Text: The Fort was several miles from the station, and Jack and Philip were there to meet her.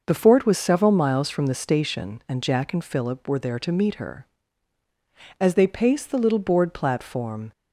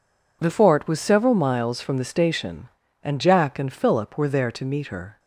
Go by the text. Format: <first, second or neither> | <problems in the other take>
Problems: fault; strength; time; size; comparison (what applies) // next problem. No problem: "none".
second | starts louder than the rest; noticeable; until 1.0 s; 6 dB // goes on to say "As they paced the little board platform"; strong; from 5.3 s on; 2.1 s long